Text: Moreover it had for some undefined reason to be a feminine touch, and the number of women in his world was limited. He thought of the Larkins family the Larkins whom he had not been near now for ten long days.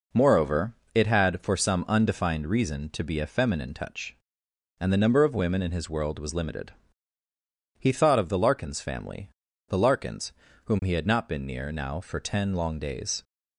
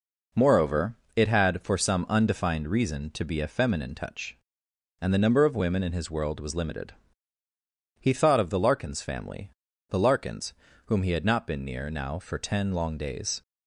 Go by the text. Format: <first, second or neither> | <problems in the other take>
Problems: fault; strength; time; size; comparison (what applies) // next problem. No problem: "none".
neither | pauses between "Moreover" and "it"; slight; the same in both // pauses between "family" and "the"; the same in both // pauses between "Larkins" and "whom"; slight; the same in both